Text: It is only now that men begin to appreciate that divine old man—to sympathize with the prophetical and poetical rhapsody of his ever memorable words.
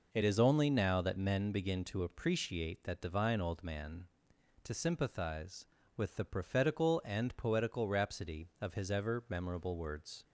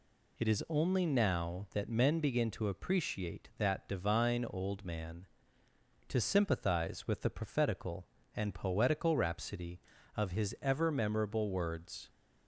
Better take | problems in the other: neither | none

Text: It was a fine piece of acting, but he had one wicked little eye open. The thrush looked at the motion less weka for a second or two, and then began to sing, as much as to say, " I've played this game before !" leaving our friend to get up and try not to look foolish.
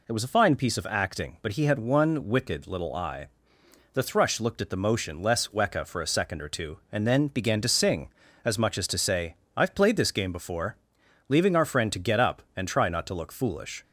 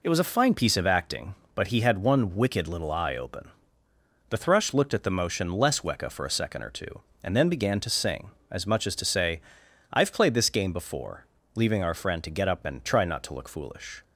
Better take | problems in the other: second | skips "open"; at 3.6 s

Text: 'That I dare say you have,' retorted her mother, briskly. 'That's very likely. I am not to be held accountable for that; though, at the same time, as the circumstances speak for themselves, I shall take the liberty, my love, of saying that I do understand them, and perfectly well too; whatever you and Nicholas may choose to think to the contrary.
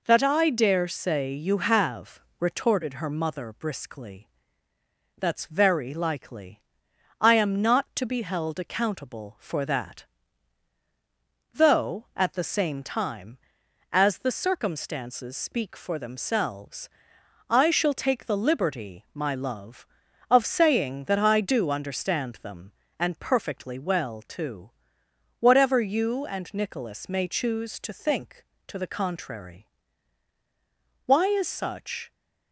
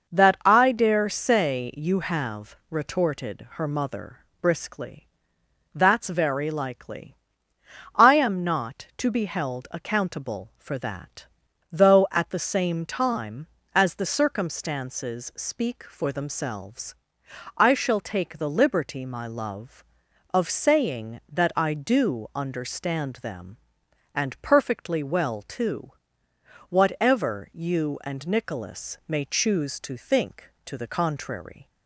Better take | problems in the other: second | goes on to say "Why is such"; noticeable; from 31.0 s on; 1.0 s long

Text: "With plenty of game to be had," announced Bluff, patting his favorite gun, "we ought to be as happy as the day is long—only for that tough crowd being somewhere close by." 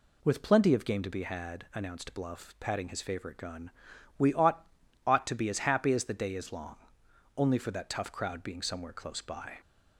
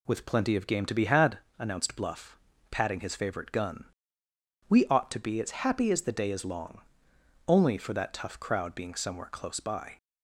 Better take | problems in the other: second | says "ought" twice; at 5.0 s

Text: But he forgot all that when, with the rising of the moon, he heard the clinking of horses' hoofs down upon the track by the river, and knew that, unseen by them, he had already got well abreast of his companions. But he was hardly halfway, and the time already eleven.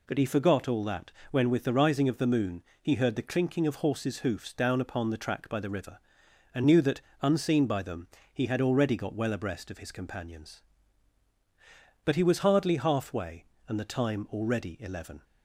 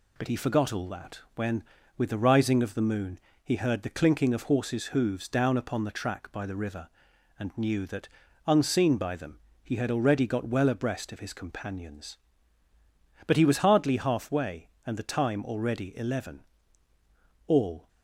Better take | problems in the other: first | pauses between "that" and "when"; slight; at 1.1 s; 0.16 s long; slight in the first // goes on to say "All"; slight; from 17.4 s on; 0.40 s long

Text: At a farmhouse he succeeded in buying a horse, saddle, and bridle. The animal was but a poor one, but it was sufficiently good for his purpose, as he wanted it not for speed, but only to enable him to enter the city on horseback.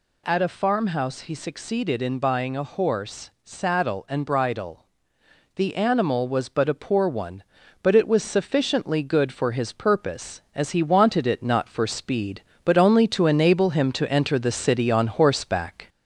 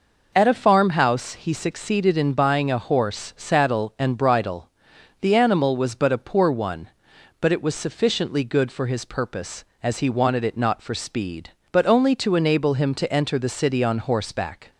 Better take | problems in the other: second | gets louder; slight; throughout; 2.5 dB

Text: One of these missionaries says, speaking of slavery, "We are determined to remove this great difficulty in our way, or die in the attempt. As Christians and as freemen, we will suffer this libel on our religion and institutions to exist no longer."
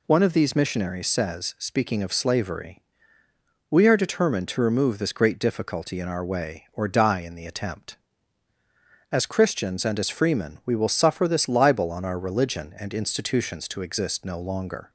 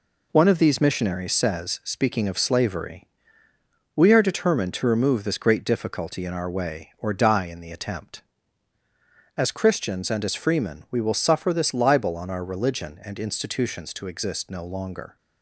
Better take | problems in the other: first | gets quieter; noticeable; throughout; 5.5 dB

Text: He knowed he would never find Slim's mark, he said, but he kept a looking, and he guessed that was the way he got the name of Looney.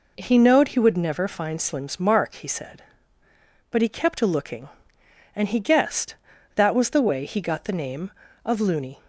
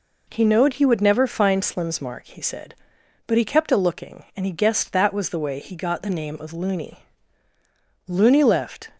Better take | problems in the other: first | goes on to say "Looney left"; noticeable; from 8.0 s on; 0.82 s long

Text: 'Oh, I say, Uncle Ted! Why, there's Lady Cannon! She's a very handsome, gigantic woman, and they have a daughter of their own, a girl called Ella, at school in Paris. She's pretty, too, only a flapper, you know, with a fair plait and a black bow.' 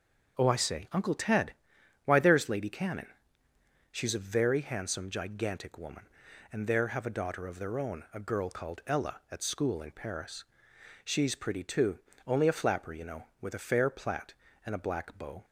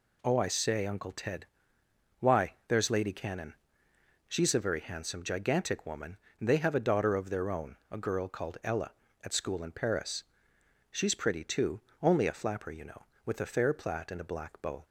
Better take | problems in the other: second | starts louder than the rest; until 1.4 s; 6.5 dB // says "there" for "they"; at 6.6 s

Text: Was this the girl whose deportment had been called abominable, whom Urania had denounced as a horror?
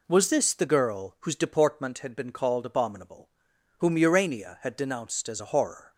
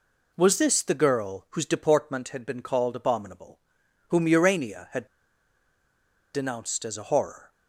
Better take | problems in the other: first | pauses between "had" and "denounced"; strong; at 5.0 s; 1.2 s long

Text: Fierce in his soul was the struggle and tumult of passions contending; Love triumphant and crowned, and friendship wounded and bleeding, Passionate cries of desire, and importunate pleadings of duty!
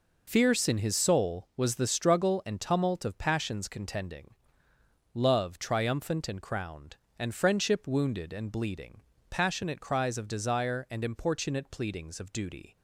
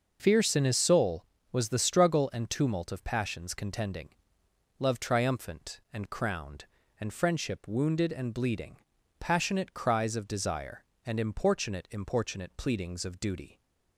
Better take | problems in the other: first | says "importunate" twice; at 11.8 s

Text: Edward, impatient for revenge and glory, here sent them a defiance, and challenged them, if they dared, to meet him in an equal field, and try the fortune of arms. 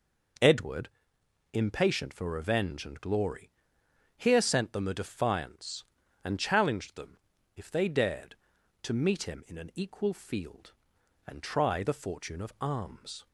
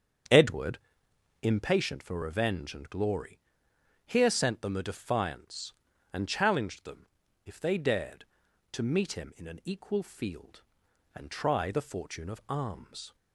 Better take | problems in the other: first | starts louder than the rest; strong; until 1.8 s; 8 dB

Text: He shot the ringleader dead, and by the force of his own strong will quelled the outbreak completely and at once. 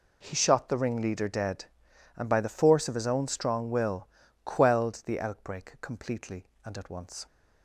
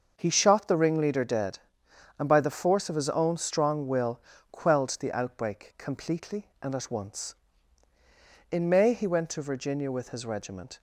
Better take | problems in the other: first | starts louder than the rest; until 1.1 s; 6 dB // pauses between "will" and "quelled"; slight; at 4.2 s; 0.28 s long; also in the first // goes on to say "In May he went to Virginia with his regiment"; strong; from 8.4 s on; 2.3 s long

